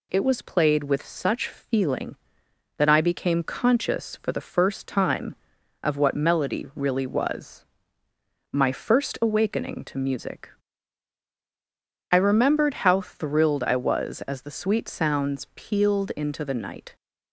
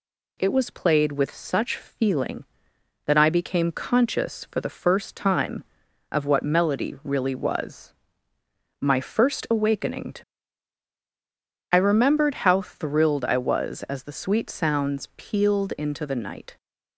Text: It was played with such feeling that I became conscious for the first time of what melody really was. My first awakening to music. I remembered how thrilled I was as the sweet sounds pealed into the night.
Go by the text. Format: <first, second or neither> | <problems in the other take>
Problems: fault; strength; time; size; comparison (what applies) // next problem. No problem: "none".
first | skips "music"; at 10.9 s